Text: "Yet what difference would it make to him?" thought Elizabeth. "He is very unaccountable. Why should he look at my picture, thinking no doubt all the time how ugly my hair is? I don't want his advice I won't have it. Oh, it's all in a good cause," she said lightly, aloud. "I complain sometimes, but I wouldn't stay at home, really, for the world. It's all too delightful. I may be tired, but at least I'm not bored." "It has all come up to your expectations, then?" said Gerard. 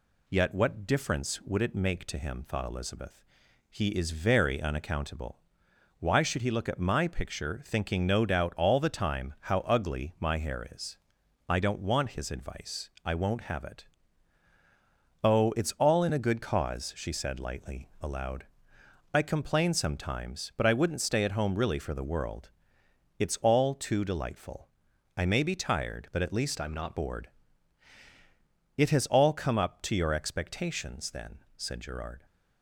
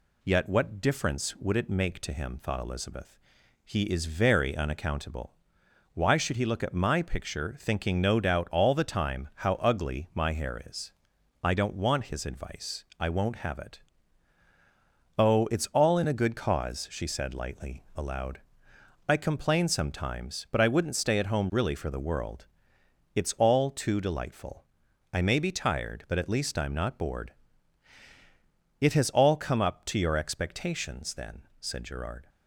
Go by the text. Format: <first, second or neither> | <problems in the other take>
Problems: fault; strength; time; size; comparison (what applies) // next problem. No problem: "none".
second | changes voice from "I'm" to "not"; from 26.5 to 26.9 s; 0.4 s long